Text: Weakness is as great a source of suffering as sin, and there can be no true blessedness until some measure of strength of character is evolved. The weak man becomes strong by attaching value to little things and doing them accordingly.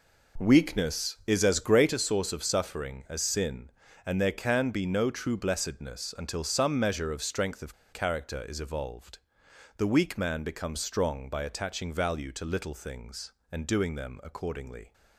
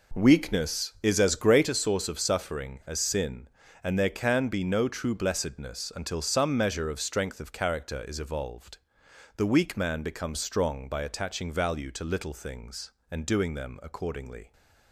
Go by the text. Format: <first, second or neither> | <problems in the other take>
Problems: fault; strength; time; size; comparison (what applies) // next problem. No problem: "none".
second | pauses between "of" and "character"; slight; at 7.7 s; 0.20 s long